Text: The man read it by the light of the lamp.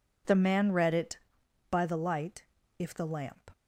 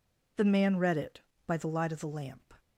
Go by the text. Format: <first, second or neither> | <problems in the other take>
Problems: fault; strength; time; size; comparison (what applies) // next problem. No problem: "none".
second | says "if" for "of"; at 2.7 s